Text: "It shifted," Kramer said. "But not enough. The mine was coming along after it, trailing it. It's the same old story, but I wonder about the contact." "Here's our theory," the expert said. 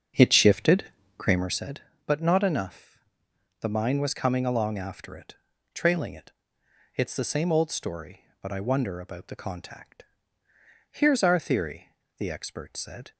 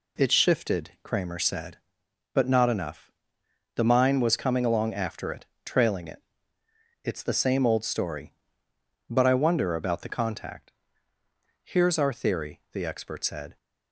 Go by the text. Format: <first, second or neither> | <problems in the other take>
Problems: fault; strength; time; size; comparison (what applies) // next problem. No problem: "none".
second | starts louder than the rest; until 1.6 s; 7 dB